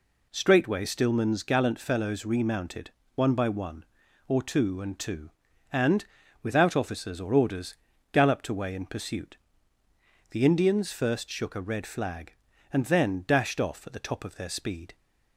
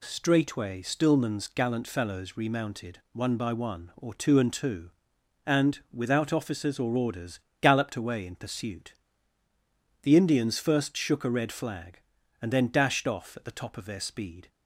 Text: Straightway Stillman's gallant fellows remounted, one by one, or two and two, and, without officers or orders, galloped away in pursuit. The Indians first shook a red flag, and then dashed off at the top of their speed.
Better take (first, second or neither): neither